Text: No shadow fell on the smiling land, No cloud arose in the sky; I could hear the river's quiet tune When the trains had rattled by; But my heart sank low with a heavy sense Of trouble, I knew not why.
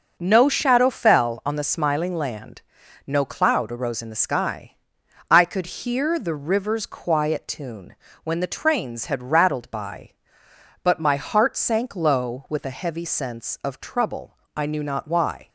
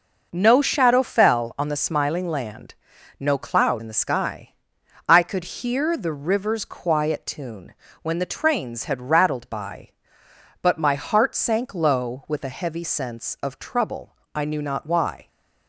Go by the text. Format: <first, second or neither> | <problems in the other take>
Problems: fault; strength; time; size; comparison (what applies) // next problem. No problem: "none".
first | skips "arose"; at 3.8 s // pauses between "tune" and "When"; slight; at 7.7 s; 0.26 s long; slight in the first